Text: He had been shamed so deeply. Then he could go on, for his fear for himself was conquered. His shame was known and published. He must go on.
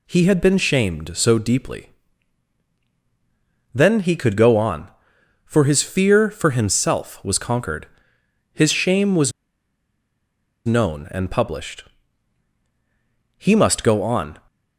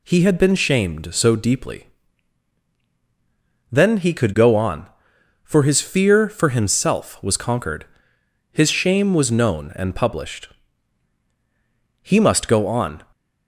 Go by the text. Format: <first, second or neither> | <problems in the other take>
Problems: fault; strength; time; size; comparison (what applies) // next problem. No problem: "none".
second | pauses between "was" and "known"; strong; at 9.3 s; 1.3 s long